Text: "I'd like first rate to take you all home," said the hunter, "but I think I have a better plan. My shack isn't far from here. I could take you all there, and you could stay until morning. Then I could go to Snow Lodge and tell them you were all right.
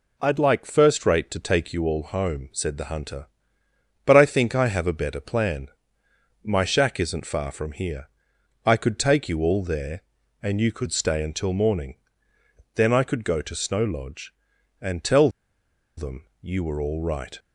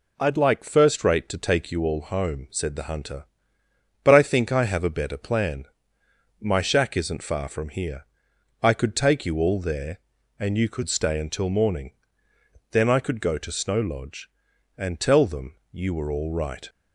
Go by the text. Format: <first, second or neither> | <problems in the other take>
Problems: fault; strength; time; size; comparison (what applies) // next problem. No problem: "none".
second | pauses between "tell" and "them"; noticeable; at 15.2 s; 0.68 s long // pauses between "them" and "you"; slight; at 16.2 s; 0.16 s long; slight in the second